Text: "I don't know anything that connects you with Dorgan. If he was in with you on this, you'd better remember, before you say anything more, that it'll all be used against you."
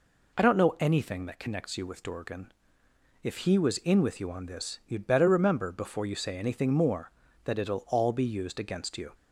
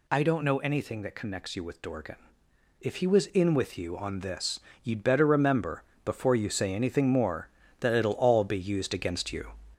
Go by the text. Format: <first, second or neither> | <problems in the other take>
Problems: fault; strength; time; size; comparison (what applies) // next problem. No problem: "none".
first | gets louder; noticeable; throughout; 4.5 dB